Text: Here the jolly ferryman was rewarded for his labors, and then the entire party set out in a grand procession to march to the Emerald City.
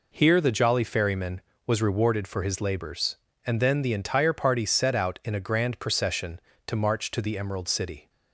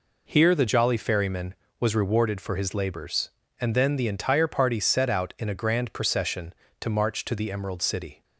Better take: neither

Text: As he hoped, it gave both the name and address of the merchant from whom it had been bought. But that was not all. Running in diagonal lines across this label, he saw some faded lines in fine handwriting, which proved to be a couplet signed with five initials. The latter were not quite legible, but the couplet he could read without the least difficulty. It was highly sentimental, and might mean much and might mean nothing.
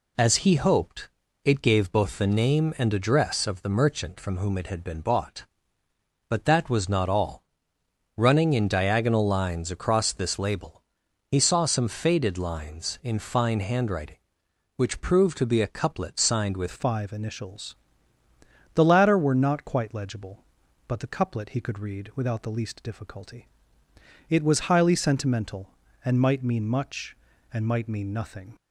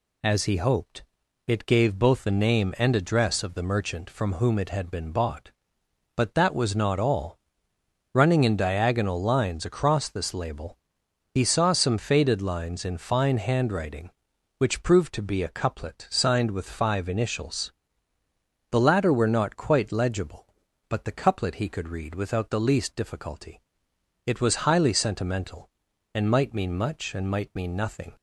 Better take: second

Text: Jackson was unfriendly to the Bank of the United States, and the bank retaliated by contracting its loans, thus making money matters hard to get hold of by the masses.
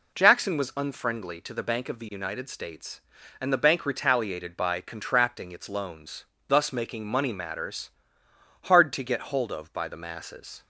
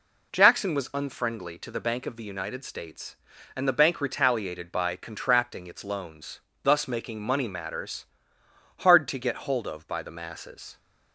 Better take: neither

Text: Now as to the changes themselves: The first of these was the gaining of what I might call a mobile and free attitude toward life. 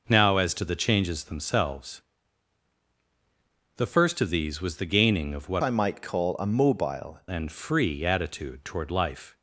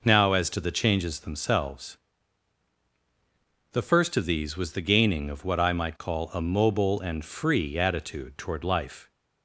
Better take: second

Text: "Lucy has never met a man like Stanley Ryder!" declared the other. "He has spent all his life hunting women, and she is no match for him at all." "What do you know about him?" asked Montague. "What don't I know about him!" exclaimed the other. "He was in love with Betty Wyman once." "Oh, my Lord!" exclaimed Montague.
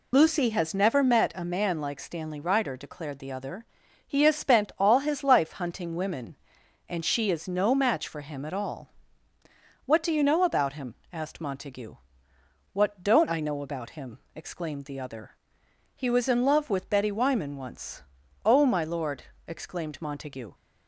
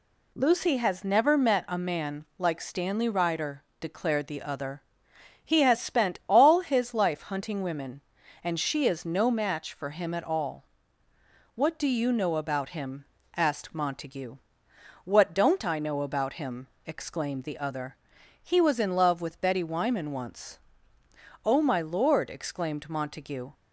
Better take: second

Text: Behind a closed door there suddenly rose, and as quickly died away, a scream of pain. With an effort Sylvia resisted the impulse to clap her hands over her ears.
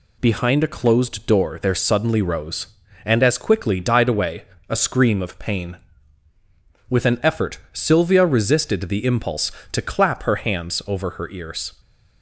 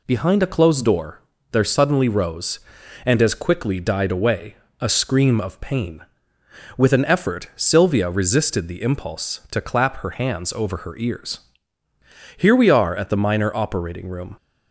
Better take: first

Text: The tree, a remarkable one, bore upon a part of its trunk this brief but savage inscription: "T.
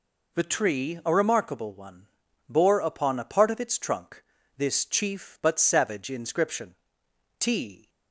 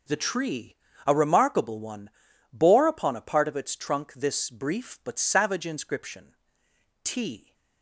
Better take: second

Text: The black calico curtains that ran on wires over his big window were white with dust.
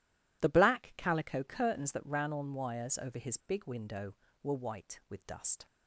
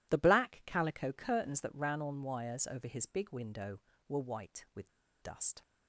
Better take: first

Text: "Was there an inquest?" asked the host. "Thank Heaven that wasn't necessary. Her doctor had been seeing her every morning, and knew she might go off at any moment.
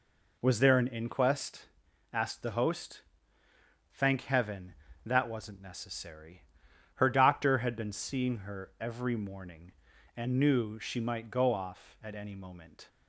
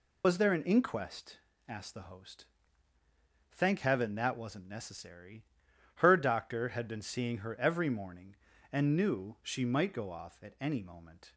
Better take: first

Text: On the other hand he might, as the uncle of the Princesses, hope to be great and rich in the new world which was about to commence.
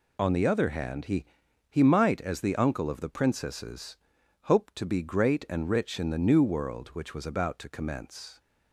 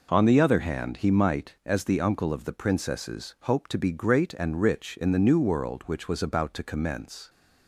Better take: second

